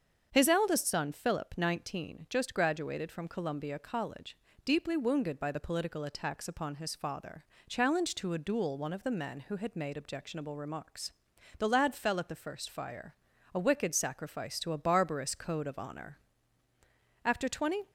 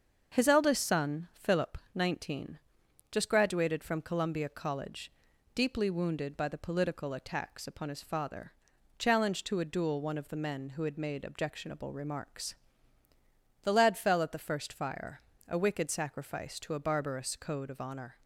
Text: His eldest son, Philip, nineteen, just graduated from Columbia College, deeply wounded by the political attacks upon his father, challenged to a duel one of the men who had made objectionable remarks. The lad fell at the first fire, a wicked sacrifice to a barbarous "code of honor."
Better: second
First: starts louder than the rest; until 1.3 s; 7 dB // goes on to say "After twenty"; noticeable; from 17.2 s on; 0.66 s long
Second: starts louder than the rest; until 1.4 s; 6.5 dB

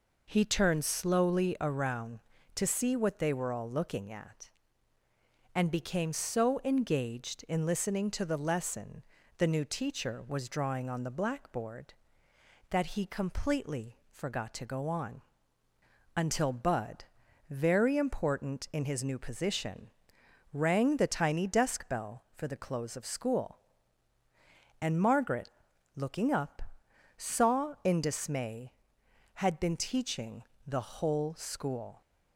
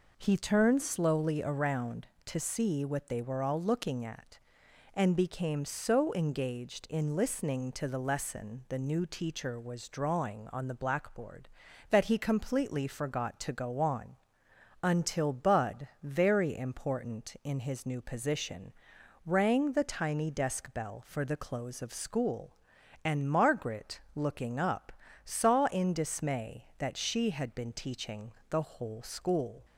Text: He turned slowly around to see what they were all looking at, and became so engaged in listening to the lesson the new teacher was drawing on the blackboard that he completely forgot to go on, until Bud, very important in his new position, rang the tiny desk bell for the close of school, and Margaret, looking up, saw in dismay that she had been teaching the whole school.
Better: second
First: pauses between "lesson" and "the"; at 9.0 s; 0.38 s long // skips "that she"; at 29.0 s // pauses between "teaching" and "the"; slight; at 30.4 s; 0.24 s long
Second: pauses between "teaching" and "the"; slight; at 28.3 s; 0.18 s long

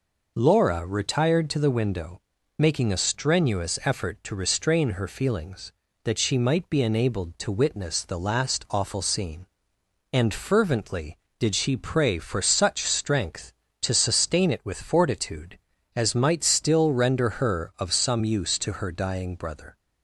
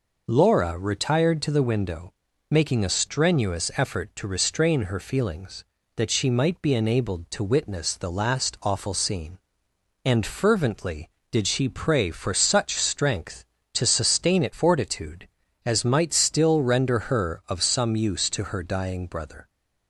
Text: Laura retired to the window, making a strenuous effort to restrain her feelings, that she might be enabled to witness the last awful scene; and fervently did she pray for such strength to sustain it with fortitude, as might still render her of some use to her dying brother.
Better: first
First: none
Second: skips "with"; at 14.5 s

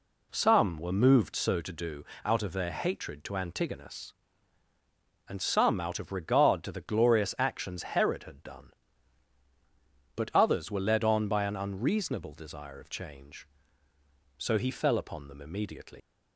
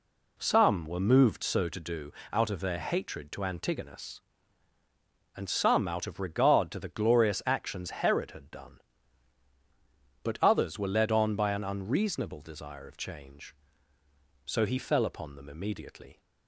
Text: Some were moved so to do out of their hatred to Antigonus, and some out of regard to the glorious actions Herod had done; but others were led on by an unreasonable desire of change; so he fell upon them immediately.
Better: second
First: pauses between "do" and "out"; slight; at 2.0 s; 0.20 s long // leaves "immediately" unfinished; at 16.0 s; 120 ms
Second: pauses between "do" and "out"; slight; at 2.1 s; 0.20 s long

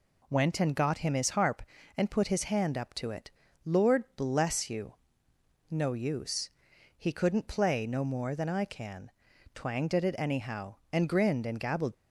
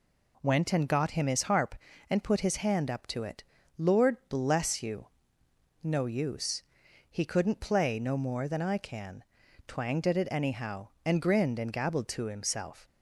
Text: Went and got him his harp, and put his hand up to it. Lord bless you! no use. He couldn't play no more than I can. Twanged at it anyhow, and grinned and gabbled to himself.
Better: second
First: stops before "to himself"; at 11.9 s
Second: none

